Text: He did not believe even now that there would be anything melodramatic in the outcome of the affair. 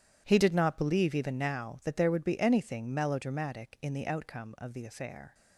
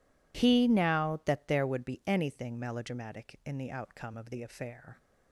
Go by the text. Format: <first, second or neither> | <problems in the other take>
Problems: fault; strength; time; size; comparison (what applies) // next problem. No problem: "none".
first | skips "did not believe even"; at 0.6 s